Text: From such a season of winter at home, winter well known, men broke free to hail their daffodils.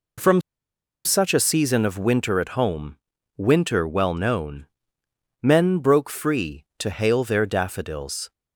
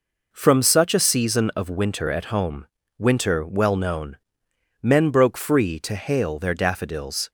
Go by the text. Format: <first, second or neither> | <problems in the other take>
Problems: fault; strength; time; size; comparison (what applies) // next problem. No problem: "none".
second | pauses between "From" and "such"; noticeable; at 0.4 s; 0.64 s long